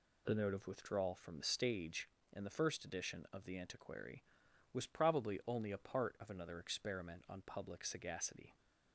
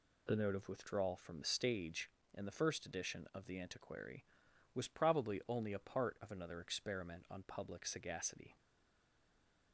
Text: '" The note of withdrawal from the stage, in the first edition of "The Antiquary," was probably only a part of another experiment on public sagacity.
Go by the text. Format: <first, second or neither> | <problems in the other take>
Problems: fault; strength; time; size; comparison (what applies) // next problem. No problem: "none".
first | stays silent after the last word; noticeable; from 8.5 s on; 1.2 s long